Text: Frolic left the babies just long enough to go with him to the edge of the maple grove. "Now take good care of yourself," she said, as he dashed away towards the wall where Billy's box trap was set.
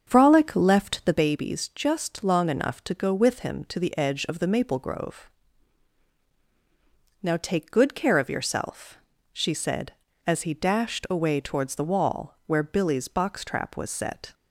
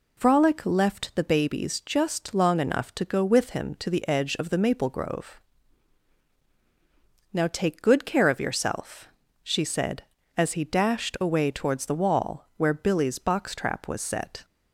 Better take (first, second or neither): second